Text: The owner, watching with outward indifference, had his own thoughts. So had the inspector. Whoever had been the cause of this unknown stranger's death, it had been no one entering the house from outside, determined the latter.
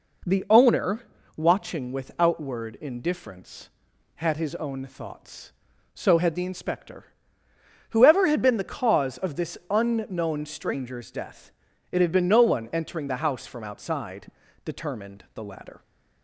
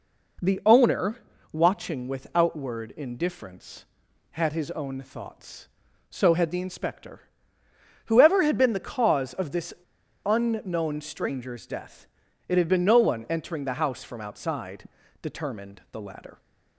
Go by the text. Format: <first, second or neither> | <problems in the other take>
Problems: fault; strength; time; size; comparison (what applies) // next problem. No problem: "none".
first | pauses between "this" and "unknown"; noticeable; at 9.7 s; 0.51 s long